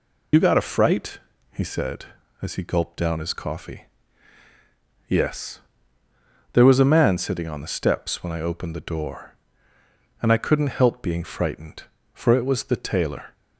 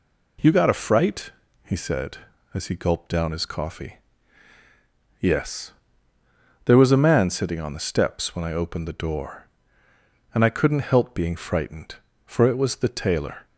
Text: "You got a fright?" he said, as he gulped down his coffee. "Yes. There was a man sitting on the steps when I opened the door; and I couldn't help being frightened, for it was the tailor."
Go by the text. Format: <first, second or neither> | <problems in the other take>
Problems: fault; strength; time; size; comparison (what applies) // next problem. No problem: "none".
second | loses the start of "You"; at 0.3 s; 70 ms